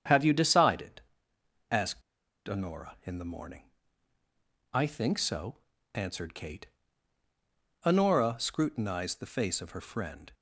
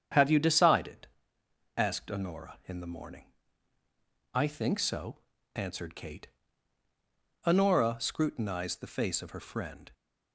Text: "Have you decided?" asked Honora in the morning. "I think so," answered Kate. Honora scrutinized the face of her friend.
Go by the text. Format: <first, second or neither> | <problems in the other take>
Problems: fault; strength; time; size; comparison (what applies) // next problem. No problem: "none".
second | starts louder than the rest; strong; until 1.8 s; 7.5 dB; strong in the second // pauses between "asked" and "Honora"; noticeable; at 2.0 s; 0.46 s long